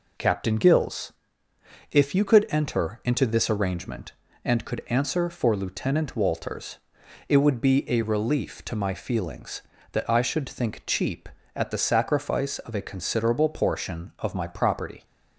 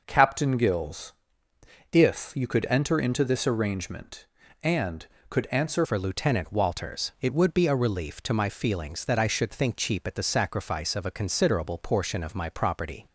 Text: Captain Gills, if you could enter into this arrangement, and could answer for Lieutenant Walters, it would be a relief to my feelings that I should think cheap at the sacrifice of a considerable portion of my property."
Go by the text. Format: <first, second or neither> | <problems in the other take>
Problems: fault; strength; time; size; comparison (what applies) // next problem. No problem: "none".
first | changes voice at "for"; from 5.8 s on; 7.2 s long